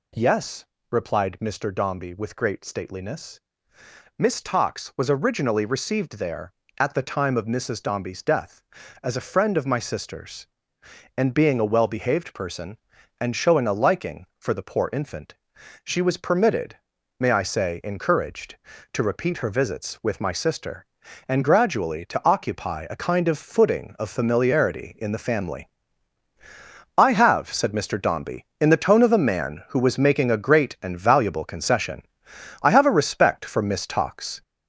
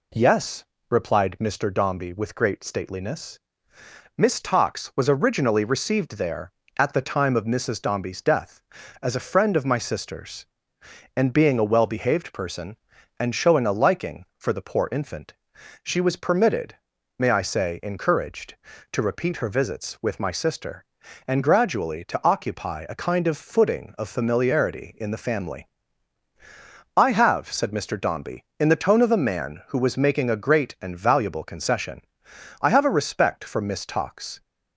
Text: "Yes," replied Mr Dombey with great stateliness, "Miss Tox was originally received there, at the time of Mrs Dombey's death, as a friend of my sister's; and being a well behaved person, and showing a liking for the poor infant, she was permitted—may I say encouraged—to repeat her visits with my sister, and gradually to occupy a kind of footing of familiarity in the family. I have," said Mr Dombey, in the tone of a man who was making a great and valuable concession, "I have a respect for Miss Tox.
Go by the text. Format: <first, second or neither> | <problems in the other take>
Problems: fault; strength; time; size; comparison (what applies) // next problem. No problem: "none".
second | gets louder; noticeable; throughout; 5.5 dB